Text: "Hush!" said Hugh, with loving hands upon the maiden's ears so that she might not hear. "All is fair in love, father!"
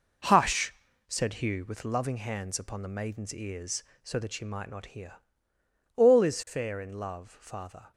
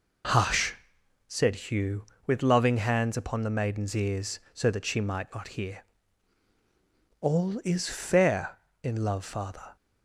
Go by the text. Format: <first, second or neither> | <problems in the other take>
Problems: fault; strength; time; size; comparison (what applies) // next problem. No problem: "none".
second | gets quieter; strong; throughout; 8.5 dB